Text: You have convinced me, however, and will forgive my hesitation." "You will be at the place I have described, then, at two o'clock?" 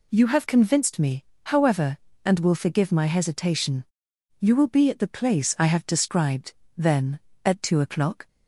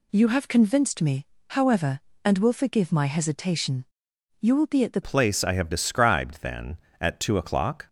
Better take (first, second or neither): first